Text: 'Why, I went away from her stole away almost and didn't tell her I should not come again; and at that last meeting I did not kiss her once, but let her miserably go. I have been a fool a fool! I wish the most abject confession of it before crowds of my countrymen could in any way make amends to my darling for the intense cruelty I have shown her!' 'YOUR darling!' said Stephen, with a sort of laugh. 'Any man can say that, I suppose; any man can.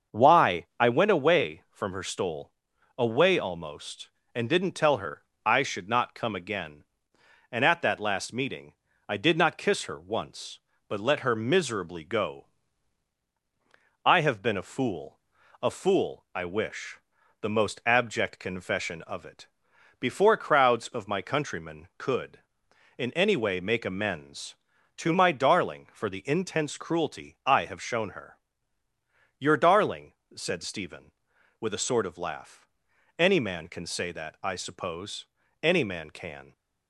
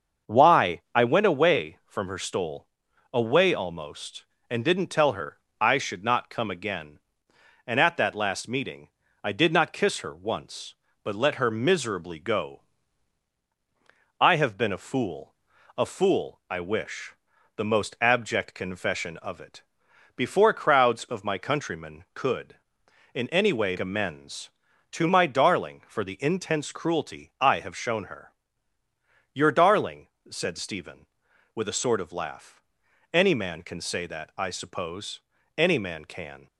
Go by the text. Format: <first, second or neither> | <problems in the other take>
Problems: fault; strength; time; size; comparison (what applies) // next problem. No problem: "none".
first | starts louder than the rest; until 1.3 s; 6.5 dB; also in the first // pauses between "stole" and "away"; noticeable; at 2.6 s; 0.46 s long; noticeable in the first // pauses between "her" and "I"; slight; at 5.3 s; 0.22 s long; slight in the first // pauses between "meeting" and "I"; slight; at 8.8 s; 0.34 s long; slight in the first // pauses between "fool" and "a"; at 15.3 s; 0.44 s long; also in the first // pauses between "wish" and "the"; at 17.1 s; 0.40 s long; also in the first // pauses between "it" and "before"; noticeable; at 19.6 s; 0.54 s long; noticeable in the first // skips "make"; at 23.7 s